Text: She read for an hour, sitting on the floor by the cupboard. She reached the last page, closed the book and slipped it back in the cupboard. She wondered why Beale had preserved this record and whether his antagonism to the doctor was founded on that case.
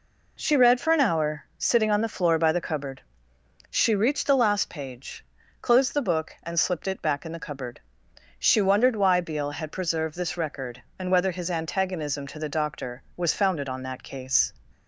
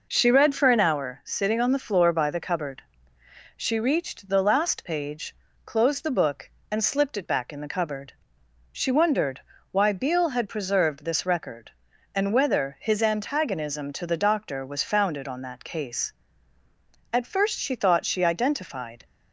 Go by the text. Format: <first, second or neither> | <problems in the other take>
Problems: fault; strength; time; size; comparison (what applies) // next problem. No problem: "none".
first | pauses between "wondered" and "why"; slight; at 9.3 s; 0.32 s long // goes on to say "At first she thought she identified"; strong; from 17.1 s on; 1.9 s long